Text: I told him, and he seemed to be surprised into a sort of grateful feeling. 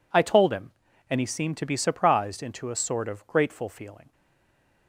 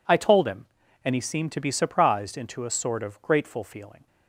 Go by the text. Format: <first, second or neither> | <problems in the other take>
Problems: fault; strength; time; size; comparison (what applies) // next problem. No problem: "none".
second | stays silent after the last word; slight; from 4.1 s on; 0.7 s long